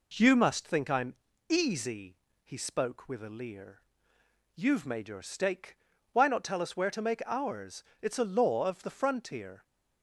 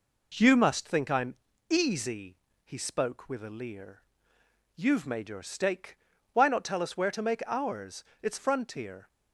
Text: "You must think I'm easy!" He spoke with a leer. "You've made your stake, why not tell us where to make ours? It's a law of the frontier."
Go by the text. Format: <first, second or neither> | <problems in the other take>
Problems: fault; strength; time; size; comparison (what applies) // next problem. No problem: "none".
first | pauses between "I'm" and "easy"; slight; at 1.3 s; 0.34 s long; slight in the first // skips "a law of the"; at 8.3 s